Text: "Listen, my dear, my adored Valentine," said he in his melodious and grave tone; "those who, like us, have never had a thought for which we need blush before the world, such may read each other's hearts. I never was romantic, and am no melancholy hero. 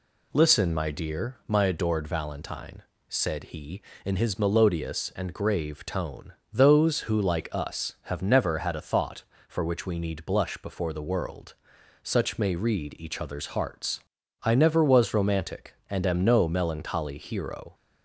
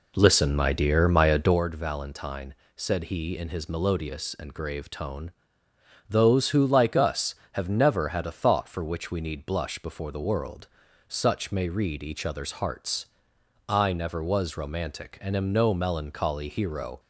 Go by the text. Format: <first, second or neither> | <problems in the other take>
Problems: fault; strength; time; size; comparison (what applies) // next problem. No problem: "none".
first | starts louder than the rest; slight; until 1.6 s; 3 dB